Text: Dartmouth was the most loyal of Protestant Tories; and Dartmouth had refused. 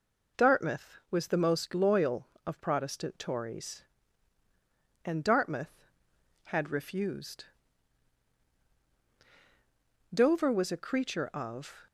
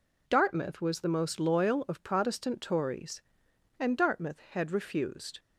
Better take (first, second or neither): second